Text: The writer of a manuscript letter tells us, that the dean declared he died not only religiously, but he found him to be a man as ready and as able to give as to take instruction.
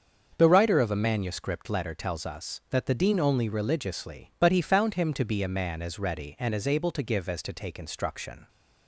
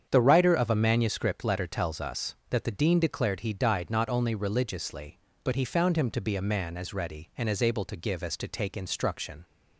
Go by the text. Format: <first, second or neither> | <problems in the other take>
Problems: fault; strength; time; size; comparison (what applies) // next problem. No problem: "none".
second | starts louder than the rest; until 1.3 s; 6.5 dB; strong in the second // skips "declared he died not"; at 3.1 s